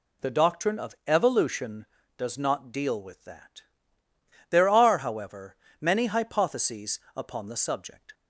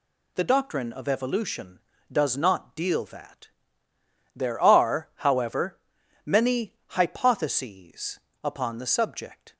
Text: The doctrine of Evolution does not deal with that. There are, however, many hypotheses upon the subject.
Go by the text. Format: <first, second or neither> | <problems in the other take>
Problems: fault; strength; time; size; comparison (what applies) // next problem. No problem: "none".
first | skips "with"; at 3.0 s // pauses between "hypotheses" and "upon"; slight; at 8.1 s; 0.24 s long; slight in the first